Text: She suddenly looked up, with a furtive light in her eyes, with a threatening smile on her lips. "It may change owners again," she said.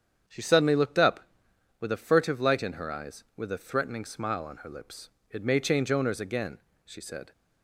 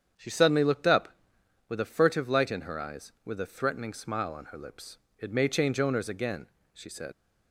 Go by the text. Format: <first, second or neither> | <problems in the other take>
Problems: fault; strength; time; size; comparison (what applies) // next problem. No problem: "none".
first | starts louder than the rest; strong; until 1.7 s; 8 dB; strong in the first // leaves "said" unfinished; at 7.1 s; 75 ms